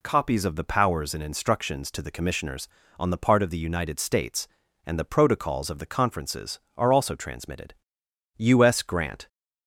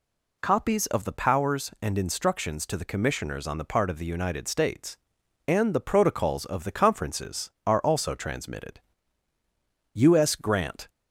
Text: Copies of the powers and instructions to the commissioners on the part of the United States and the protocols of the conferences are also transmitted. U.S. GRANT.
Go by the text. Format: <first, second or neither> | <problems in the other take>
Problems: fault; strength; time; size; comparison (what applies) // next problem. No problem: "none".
neither | none